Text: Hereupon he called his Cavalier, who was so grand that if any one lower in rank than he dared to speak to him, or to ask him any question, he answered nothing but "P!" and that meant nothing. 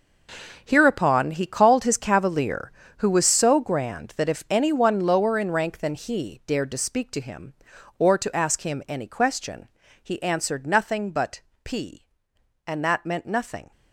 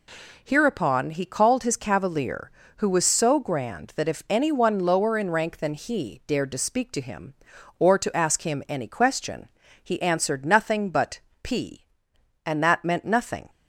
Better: second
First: gets quieter; strong; throughout; 12 dB // pauses between "but" and "P"; slight; at 11.4 s; 0.24 s long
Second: pauses between "but" and "P"; slight; at 11.1 s; 0.24 s long

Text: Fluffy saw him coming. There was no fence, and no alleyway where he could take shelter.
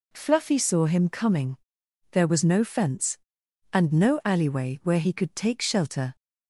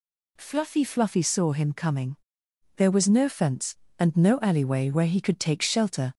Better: first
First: none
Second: says "Fluffy" twice; at 0.8 s

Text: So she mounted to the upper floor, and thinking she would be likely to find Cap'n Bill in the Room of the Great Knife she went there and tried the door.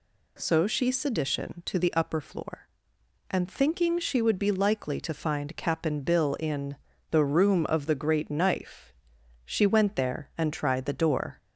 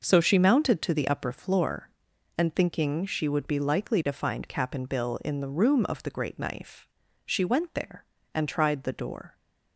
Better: second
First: says "sedition" for "mounted"; at 0.9 s // pauses between "in" and "the"; slight; at 6.7 s; 0.34 s long // pauses between "Knife" and "she"; noticeable; at 8.9 s; 0.56 s long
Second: pauses between "Knife" and "she"; at 6.8 s; 0.40 s long

